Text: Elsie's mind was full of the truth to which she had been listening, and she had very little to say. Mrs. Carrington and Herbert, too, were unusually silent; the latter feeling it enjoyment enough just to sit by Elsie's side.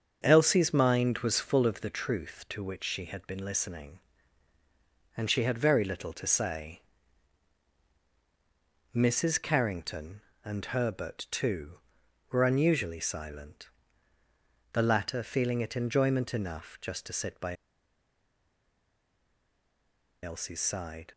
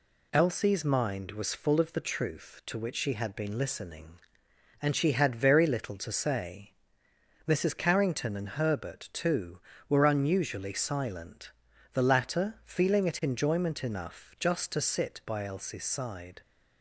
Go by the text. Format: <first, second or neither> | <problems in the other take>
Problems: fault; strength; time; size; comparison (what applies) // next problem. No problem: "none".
second | starts louder than the rest; until 1.2 s; 6.5 dB // pauses between "by" and "Elsie's"; strong; at 17.5 s; 2.6 s long